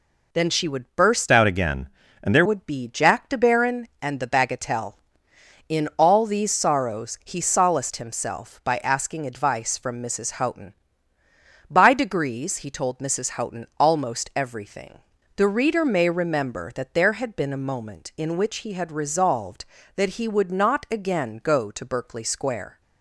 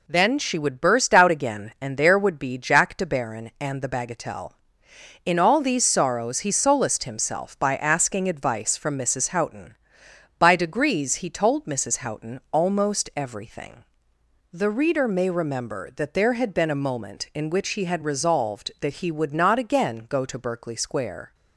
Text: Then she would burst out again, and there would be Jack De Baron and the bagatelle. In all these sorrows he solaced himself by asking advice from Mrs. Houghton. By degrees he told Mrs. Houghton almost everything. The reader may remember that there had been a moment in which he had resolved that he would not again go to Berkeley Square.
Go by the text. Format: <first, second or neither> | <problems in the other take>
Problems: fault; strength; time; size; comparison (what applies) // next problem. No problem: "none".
second | changes voice from "out" to "there"; from 1.3 to 2.4 s; 1.1 s long